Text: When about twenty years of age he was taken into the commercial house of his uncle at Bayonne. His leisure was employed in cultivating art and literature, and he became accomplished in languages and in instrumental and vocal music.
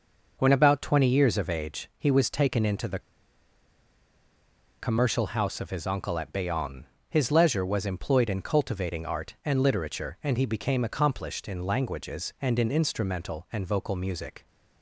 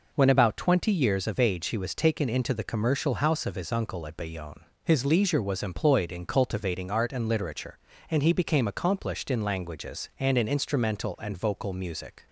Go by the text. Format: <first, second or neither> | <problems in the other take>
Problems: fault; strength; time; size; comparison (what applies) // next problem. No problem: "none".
second | pauses between "the" and "commercial"; strong; at 2.9 s; 1.8 s long